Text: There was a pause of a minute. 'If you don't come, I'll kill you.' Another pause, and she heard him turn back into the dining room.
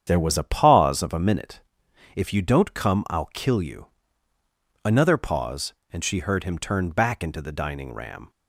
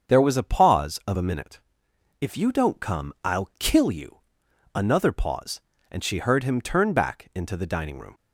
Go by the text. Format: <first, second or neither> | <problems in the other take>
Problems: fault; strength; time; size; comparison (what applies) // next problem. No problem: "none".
second | starts louder than the rest; strong; until 1.0 s; 8 dB; strong in the second // says "ram" for "room"; at 7.9 s